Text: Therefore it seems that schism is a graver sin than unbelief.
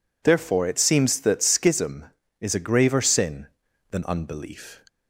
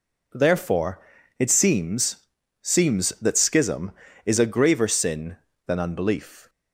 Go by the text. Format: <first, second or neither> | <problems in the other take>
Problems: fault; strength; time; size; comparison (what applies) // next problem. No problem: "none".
first | pauses between "Therefore" and "it"; at 0.9 s; 0.40 s long // says "seems" twice; at 2.6 s